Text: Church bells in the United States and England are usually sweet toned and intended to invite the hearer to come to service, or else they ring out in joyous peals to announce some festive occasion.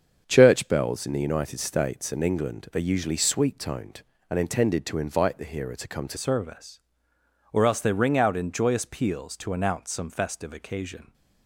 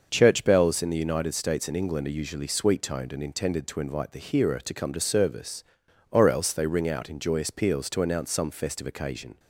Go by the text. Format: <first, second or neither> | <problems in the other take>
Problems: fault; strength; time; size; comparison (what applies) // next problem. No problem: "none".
second | starts louder than the rest; until 1.2 s; 7 dB; also in the second // changes voice at "service"; from 6.1 s on; 5.0 s long